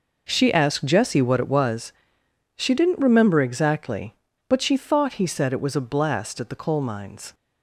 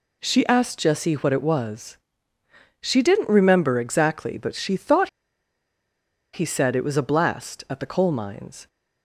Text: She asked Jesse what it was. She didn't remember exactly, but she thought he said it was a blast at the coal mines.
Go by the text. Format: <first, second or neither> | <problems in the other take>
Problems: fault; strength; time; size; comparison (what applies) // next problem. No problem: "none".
first | pauses between "thought" and "he"; at 5.0 s; 1.2 s long